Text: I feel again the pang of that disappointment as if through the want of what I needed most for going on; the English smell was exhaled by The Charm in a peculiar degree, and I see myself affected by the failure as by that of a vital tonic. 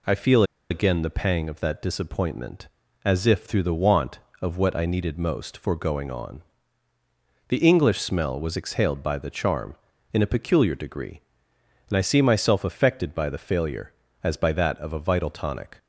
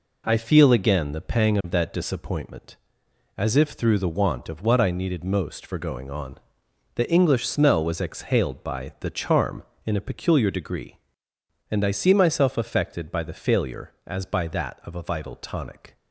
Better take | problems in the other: second | pauses between "feel" and "again"; slight; at 0.4 s; 0.26 s long

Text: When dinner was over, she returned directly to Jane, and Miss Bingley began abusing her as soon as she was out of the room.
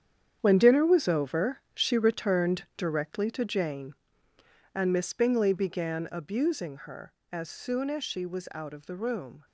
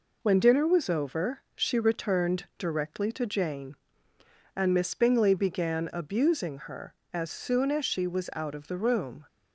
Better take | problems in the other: second | gets quieter; strong; throughout; 10.5 dB

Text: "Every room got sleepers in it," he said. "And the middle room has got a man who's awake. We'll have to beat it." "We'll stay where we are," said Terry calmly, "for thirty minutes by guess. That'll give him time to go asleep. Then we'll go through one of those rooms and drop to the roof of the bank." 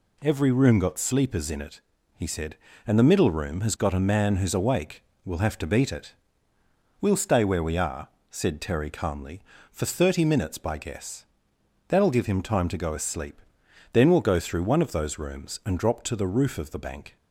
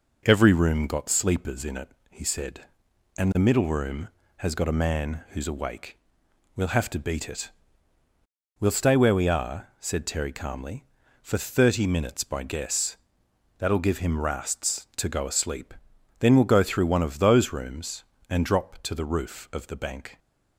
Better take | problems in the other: first | says "rasts" for "time"; at 14.1 s

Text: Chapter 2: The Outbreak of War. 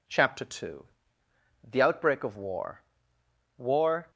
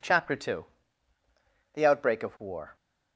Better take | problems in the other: second | says "War" twice; at 3.5 s

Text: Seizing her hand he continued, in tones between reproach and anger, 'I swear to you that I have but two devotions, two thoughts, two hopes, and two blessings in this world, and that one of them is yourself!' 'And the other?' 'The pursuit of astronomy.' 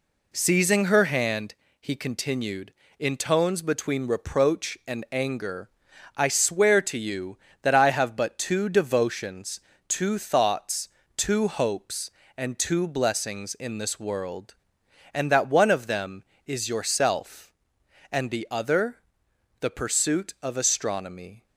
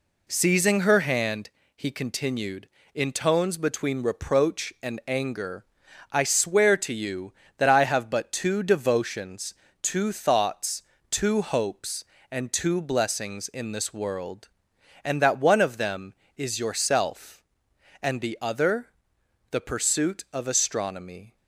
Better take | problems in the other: neither | pauses between "hand" and "he"; slight; the same in both

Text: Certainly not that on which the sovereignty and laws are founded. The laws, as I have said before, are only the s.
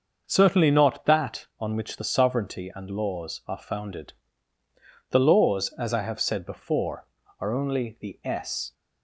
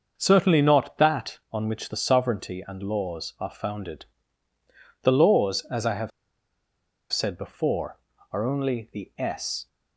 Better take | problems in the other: first | starts louder than the rest; until 1.1 s; 6.5 dB; also in the first // pauses between "have" and "said"; at 6.1 s; 1.0 s long

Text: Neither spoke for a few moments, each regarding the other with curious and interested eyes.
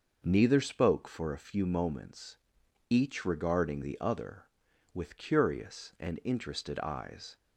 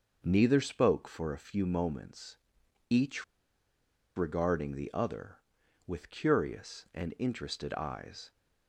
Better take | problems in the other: first | starts louder than the rest; noticeable; until 1.2 s; 6 dB; noticeable in the first // pauses between "each" and "regarding"; noticeable; at 3.2 s; 0.92 s long

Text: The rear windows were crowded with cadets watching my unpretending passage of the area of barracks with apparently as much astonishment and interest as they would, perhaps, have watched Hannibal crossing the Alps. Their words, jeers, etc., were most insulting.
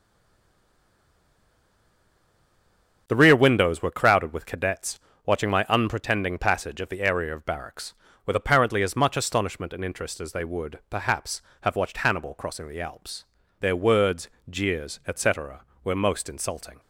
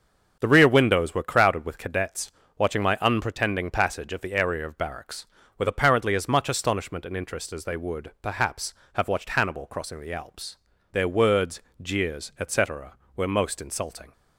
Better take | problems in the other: second | stays silent before the first word; strong; until 3.0 s; 3.0 s long // starts louder than the rest; until 4.0 s; 7 dB; also in the second // pauses between "cadets" and "watching"; slight; at 4.9 s; 0.28 s long; slight in the second

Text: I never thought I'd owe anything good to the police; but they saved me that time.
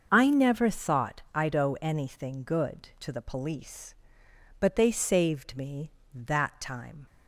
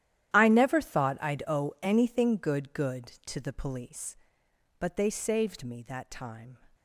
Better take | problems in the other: first | starts louder than the rest; strong; until 1.3 s; 11.5 dB; also in the first // says "good" twice; at 2.7 s

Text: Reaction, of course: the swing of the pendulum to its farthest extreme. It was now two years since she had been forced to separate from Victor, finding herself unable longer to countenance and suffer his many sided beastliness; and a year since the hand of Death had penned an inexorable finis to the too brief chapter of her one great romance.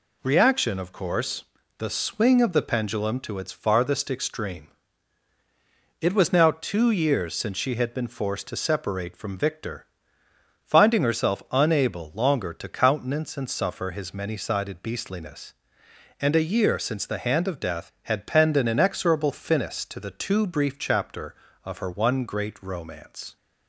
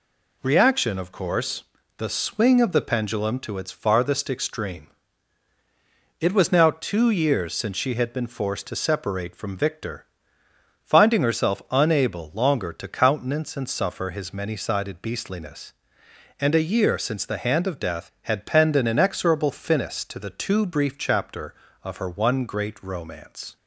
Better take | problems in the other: neither | none

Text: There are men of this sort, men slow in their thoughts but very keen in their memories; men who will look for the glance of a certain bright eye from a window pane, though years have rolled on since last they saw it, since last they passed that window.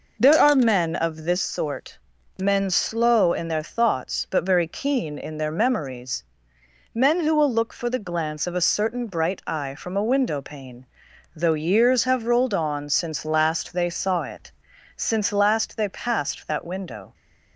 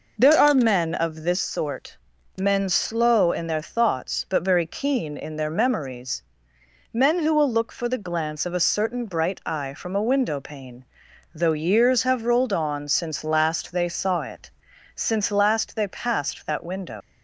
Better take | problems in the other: first | leaves "window" unfinished; at 17.0 s; 120 ms

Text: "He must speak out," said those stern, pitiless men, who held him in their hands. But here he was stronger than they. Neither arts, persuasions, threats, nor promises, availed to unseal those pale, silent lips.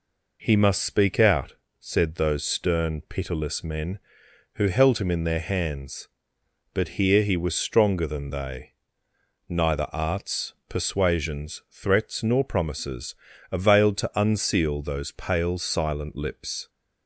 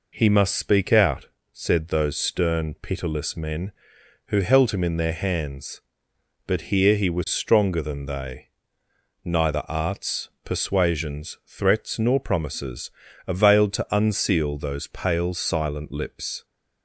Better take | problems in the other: neither | none

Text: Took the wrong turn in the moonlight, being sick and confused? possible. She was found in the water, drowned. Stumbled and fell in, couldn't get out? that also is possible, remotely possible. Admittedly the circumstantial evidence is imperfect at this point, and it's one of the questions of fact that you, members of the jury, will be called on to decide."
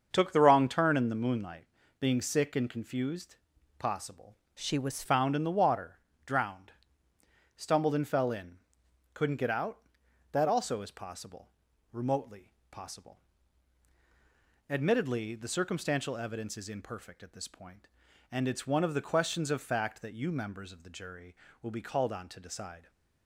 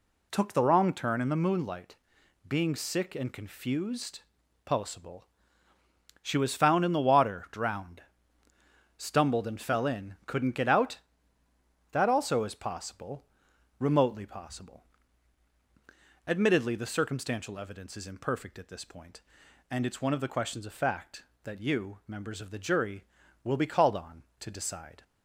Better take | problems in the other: second | starts louder than the rest; until 1.1 s; 6.5 dB // changes voice from "She" to "was"; from 4.5 to 5.0 s; 0.5 s long // pauses between "remotely" and "possible"; slight; at 12.5 s; 0.18 s long

